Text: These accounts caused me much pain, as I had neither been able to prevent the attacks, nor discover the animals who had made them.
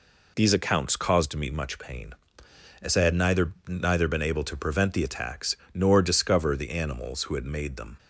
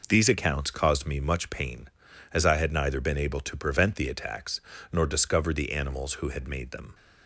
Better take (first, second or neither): second